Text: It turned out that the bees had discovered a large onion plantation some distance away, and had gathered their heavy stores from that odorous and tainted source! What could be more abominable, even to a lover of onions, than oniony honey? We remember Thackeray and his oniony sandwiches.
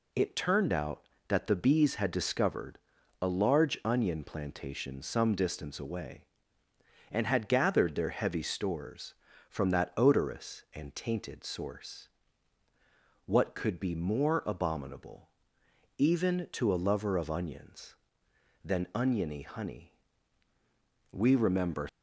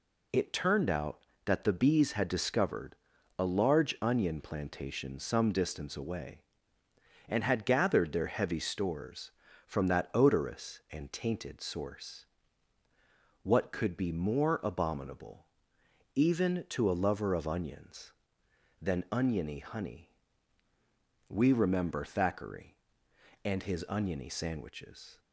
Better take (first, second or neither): second